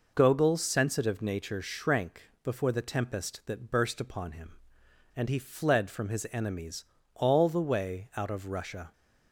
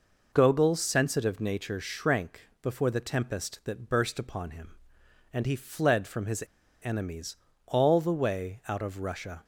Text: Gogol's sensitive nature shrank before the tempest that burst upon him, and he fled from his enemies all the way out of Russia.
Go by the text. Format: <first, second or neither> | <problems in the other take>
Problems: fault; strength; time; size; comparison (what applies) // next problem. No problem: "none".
first | pauses between "his" and "enemies"; at 6.4 s; 0.40 s long // pauses between "enemies" and "all"; slight; at 7.3 s; 0.28 s long; slight in the first